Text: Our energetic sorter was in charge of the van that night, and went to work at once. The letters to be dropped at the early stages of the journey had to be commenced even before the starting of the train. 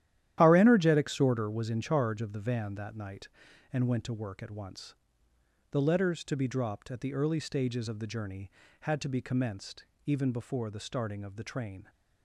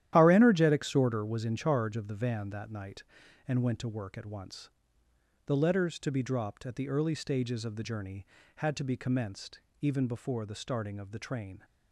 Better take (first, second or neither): neither